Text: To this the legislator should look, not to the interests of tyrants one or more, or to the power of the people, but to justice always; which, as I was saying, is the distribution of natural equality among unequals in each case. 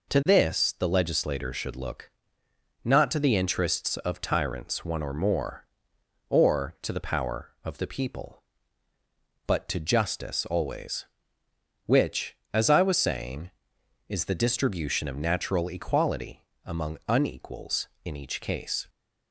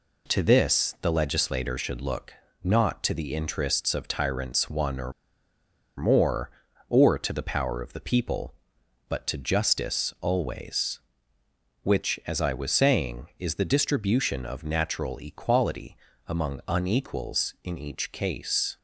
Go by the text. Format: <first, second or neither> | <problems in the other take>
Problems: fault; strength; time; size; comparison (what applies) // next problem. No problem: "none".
first | pauses between "or" and "more"; noticeable; at 5.1 s; 0.84 s long // pauses between "equality" and "among"; slight; at 15.9 s; 0.30 s long; slight in the first